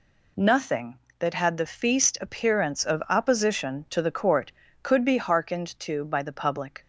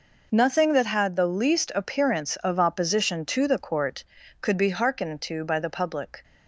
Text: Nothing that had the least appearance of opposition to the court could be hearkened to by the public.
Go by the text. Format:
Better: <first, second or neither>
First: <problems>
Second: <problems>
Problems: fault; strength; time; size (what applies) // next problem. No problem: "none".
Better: second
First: says "feast" for "least"; at 1.6 s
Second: none